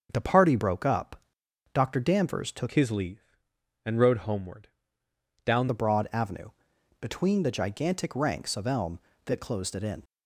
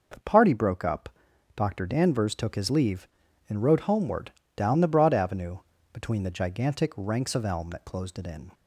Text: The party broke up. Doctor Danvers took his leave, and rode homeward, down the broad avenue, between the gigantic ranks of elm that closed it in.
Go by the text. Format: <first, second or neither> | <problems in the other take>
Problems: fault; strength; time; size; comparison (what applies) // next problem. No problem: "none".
second | starts louder than the rest; until 1.1 s; 6.5 dB // changes voice from "his" to "down"; from 2.7 to 5.6 s; 2.9 s long